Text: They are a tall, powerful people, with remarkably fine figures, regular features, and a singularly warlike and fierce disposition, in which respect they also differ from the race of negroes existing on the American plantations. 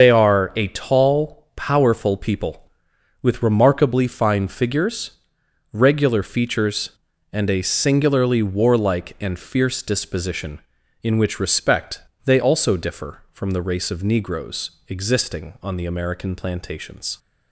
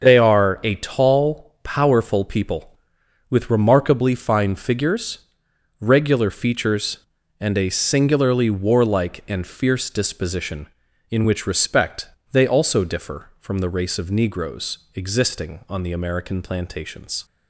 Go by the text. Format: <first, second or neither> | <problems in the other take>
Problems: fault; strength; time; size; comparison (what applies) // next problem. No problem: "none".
second | loses the start of "They"; at 0.0 s; 60 ms // starts louder than the rest; until 1.0 s; 6.5 dB; noticeable in the second // pauses between "respect" and "they"; slight; at 12.0 s; 0.24 s long; slight in the second // pauses between "negroes" and "existing"; slight; at 14.7 s; 0.18 s long; slight in the second